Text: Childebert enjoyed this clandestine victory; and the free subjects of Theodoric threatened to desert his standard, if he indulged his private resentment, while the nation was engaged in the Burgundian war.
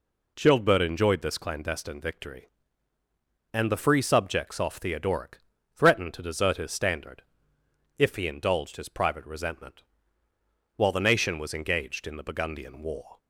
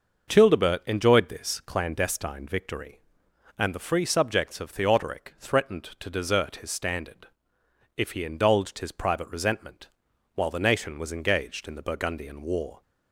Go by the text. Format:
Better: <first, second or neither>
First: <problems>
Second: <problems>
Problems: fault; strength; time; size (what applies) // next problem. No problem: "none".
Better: second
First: says "off" for "of"; at 4.5 s // pauses between "Theodoric" and "threatened"; slight; at 5.3 s; 0.34 s long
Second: none